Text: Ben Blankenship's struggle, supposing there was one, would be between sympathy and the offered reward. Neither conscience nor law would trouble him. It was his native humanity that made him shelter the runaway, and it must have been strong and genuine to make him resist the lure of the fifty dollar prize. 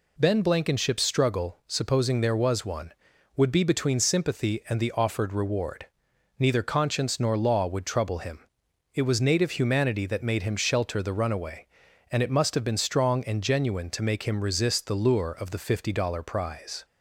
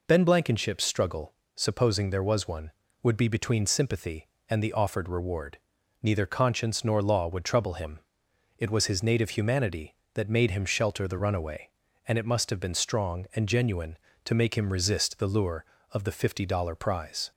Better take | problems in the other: second | skips "his"; at 9.2 s

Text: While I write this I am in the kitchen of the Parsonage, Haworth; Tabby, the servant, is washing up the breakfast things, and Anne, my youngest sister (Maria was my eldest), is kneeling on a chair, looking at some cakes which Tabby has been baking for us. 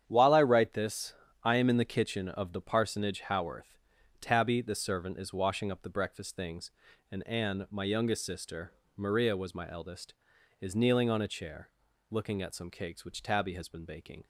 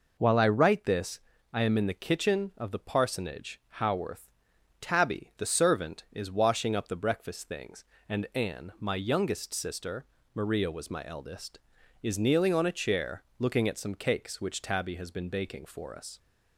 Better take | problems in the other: second | starts louder than the rest; strong; until 1.0 s; 9 dB // pauses between "this" and "I"; slight; at 1.1 s; 0.28 s long; slight in the second // stops before "for us"; at 14.2 s

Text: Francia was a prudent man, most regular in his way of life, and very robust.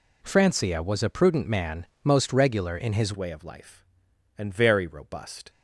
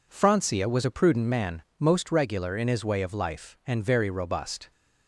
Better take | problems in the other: second | changes voice at "way"; from 3.1 s on; 2.3 s long

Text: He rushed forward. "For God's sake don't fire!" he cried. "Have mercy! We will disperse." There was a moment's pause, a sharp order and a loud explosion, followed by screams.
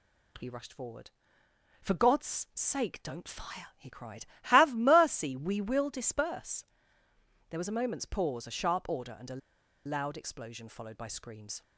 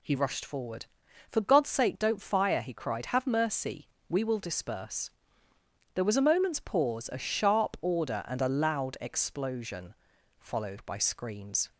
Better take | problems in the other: second | pauses between "a" and "loud"; noticeable; at 9.4 s; 0.47 s long

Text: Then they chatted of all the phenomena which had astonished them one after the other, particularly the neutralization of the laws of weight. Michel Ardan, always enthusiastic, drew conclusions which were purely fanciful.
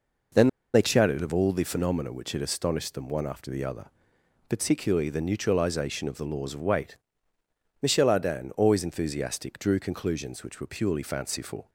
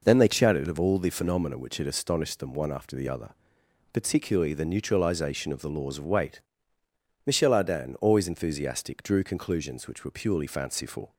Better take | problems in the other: second | pauses between "Then" and "they"; slight; at 0.4 s; 0.26 s long

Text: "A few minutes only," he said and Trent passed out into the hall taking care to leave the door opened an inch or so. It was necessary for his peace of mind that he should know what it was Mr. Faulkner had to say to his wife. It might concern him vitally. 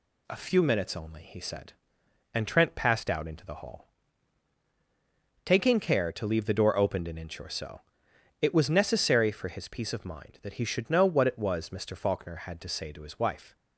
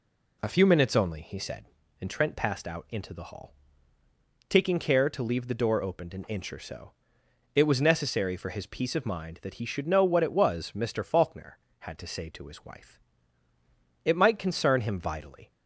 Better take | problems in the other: second | pauses between "hall" and "taking"; strong; at 3.8 s; 1.5 s long; noticeable in the second // stops before "It might concern him vitally"; at 13.5 s

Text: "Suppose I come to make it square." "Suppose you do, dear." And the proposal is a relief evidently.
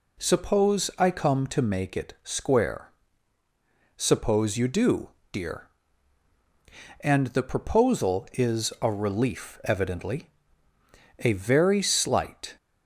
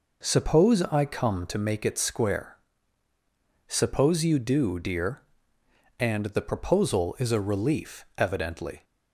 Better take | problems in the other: second | goes on to say "A very slight"; from 11.2 s on; 1.3 s long

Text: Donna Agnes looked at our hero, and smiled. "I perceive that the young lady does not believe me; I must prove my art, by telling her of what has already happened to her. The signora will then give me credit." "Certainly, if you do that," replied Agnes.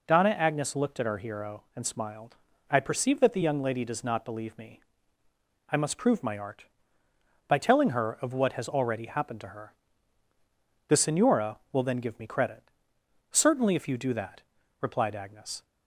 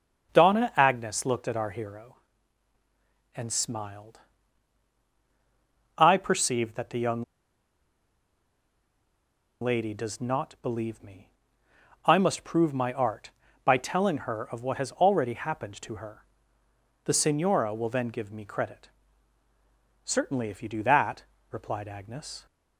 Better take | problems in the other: first | starts louder than the rest; until 1.3 s; 7 dB // pauses between "young" and "lady"; strong; at 7.2 s; 2.3 s long

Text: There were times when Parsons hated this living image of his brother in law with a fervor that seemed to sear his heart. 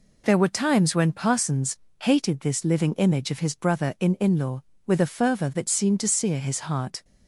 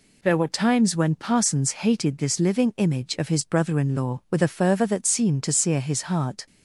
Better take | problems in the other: second | pauses between "Parsons" and "hated"; slight; at 1.7 s; 0.22 s long // says "in" twice; at 4.1 s

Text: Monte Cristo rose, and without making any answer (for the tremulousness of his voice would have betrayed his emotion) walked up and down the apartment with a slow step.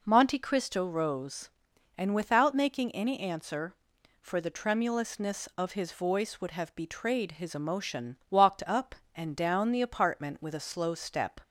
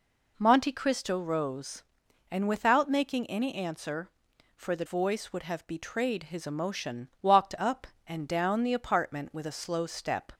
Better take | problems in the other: first | skips "tremulousness of his"; at 4.8 s

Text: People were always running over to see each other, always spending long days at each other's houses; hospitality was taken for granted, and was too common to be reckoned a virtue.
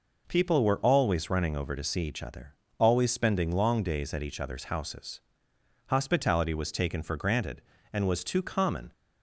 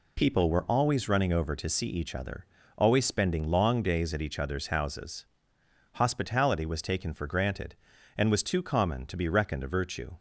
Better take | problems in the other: second | stops before "to be reckoned a virtue"; at 8.9 s

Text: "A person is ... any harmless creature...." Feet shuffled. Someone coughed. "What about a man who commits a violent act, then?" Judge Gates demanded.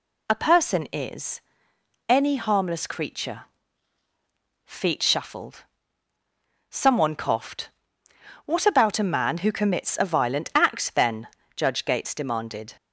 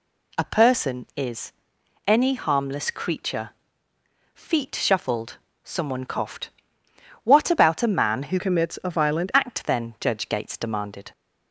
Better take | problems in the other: first | changes voice from "commits" to "violent"; from 8.3 to 9.3 s; 1.0 s long

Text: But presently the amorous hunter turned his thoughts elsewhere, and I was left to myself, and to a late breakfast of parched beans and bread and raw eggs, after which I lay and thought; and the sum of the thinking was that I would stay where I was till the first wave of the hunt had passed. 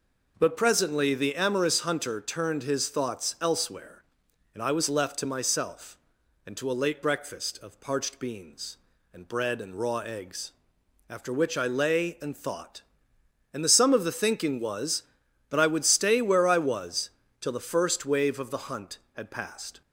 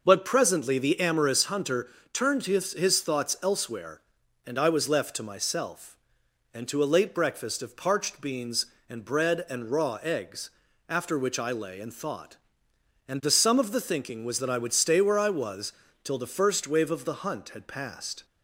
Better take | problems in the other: first | pauses between "hunter" and "turned"; slight; at 1.8 s; 0.22 s long // says "his" twice; at 2.7 s // pauses between "was" and "till"; slight; at 15.7 s; 0.30 s long; slight in the first

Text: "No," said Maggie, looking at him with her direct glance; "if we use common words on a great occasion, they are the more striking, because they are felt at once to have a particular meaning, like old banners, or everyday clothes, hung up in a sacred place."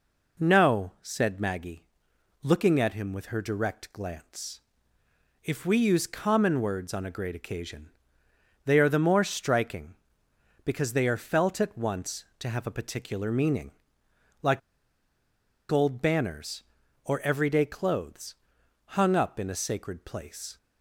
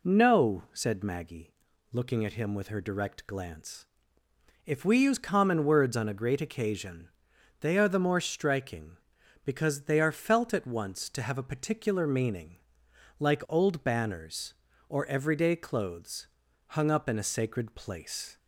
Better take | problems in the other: second | pauses between "like" and "old"; at 14.6 s; 1.1 s long

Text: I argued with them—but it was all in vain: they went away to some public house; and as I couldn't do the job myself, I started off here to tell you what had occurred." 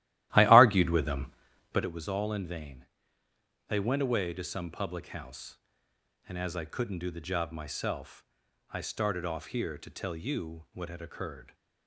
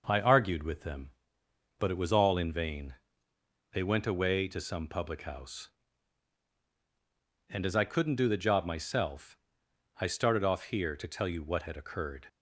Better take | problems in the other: second | starts louder than the rest; strong; until 1.9 s; 15 dB

